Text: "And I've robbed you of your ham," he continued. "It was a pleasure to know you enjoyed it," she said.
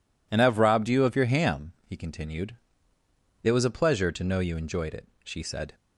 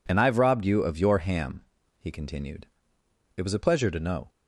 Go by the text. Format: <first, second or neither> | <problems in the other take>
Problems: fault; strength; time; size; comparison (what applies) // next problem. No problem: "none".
first | stops before "you enjoyed it she said"; at 4.2 s